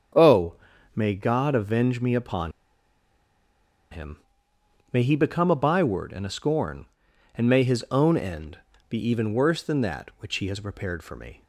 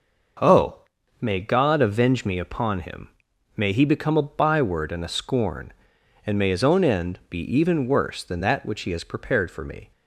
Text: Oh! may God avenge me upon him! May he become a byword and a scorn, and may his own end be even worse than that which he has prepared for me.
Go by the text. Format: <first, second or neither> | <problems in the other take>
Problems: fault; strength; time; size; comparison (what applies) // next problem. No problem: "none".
second | starts louder than the rest; strong; until 1.5 s; 7.5 dB // pauses between "upon" and "him"; strong; at 2.5 s; 1.3 s long // pauses between "end" and "be"; slight; at 8.5 s; 0.32 s long